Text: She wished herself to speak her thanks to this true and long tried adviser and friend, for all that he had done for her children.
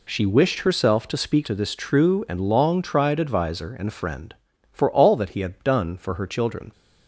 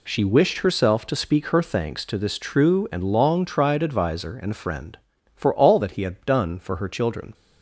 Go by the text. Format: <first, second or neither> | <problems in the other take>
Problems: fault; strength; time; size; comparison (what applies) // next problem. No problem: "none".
second | skips "her thanks"; at 1.4 s